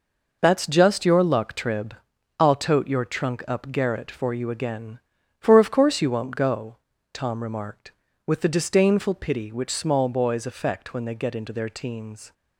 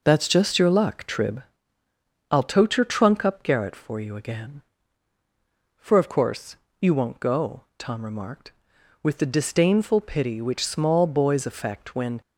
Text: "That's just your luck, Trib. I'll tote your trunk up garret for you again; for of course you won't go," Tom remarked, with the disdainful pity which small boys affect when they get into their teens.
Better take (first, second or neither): first